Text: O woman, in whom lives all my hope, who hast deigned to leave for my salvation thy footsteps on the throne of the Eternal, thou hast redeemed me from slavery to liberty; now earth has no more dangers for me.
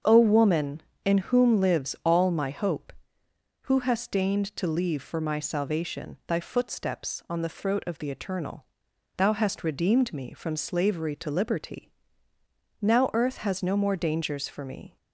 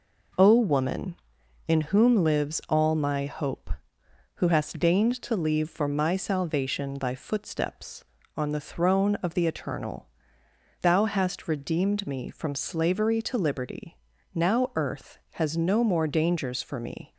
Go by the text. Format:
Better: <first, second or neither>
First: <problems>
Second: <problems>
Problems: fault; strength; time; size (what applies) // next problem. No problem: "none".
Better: second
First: starts louder than the rest; until 1.2 s; 7 dB // says "throat" for "throne"; at 7.4 s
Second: none